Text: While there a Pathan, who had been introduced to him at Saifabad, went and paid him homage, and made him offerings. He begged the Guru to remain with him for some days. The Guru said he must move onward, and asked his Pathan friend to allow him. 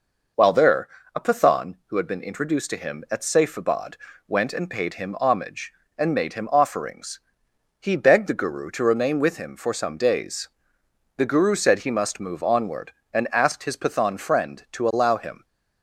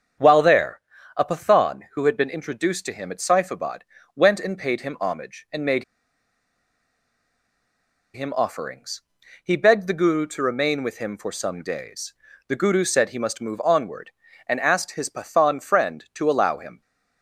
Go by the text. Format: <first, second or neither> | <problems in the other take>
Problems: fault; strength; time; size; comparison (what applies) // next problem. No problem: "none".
first | starts louder than the rest; strong; until 1.5 s; 7 dB // pauses between "there" and "a"; slight; at 0.8 s; 0.34 s long; slight in the first // pauses between "made" and "him"; strong; at 5.8 s; 2.3 s long